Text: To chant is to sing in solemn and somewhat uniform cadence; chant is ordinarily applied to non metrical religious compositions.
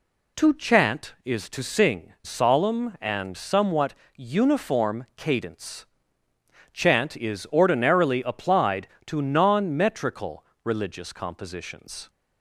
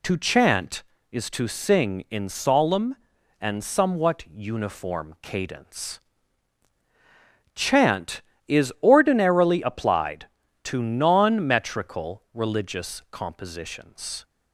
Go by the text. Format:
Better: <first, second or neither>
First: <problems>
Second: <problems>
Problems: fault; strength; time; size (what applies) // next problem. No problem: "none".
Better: second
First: skips "in"; at 2.1 s // pauses between "somewhat" and "uniform"; slight; at 3.9 s; 0.22 s long // pauses between "metrical" and "religious"; slight; at 10.4 s; 0.20 s long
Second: none